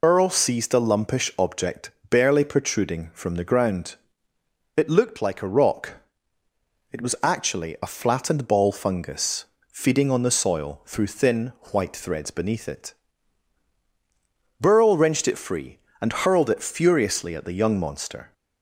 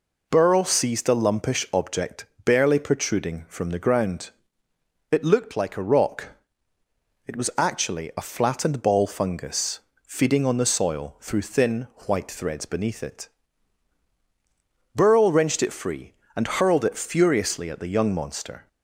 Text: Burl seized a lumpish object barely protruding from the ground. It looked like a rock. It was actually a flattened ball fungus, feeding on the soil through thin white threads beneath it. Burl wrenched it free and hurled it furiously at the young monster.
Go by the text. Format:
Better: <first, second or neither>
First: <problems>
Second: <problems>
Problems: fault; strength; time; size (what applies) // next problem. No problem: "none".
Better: second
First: loses the start of "Burl"; at 0.0 s; 85 ms // pauses between "object" and "barely"; slight; at 1.9 s; 0.18 s long // pauses between "thin" and "white"; slight; at 11.5 s; 0.20 s long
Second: pauses between "object" and "barely"; slight; at 2.2 s; 0.18 s long // pauses between "thin" and "white"; slight; at 11.8 s; 0.20 s long